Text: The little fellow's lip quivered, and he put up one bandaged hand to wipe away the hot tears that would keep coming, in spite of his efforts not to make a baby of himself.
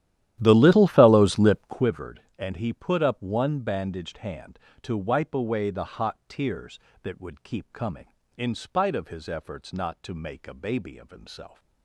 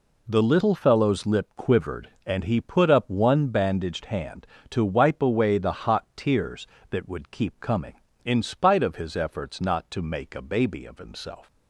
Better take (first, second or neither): second